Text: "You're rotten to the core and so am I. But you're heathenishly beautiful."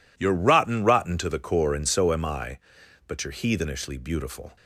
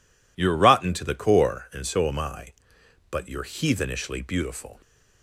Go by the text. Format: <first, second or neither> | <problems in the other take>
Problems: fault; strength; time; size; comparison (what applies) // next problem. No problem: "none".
second | says "rotten" twice; at 0.8 s